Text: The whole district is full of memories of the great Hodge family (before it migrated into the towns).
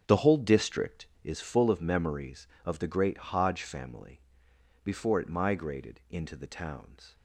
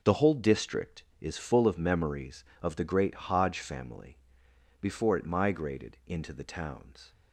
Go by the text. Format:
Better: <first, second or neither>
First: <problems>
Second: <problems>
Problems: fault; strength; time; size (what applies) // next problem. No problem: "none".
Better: second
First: starts louder than the rest; strong; until 1.4 s; 7.5 dB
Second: none